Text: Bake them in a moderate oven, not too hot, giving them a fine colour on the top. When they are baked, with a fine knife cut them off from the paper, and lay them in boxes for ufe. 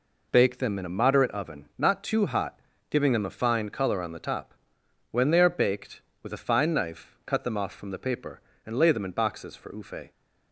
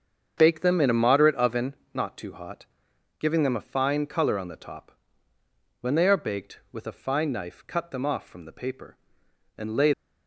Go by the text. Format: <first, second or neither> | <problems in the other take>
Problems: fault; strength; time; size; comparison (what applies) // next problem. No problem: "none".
first | starts louder than the rest; until 1.3 s; 7 dB // stops before "them in boxes for ufe"; at 9.9 s